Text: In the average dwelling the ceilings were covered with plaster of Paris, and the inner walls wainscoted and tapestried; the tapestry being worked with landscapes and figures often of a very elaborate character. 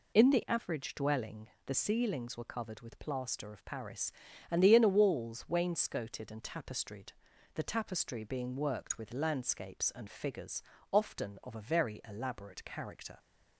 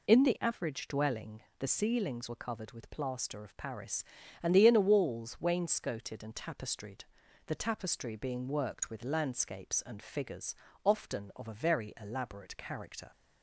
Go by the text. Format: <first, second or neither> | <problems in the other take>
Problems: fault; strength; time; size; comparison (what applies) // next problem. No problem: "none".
neither | pauses between "dwelling" and "the"; slight; the same in both // pauses between "figures" and "often"; slight; the same in both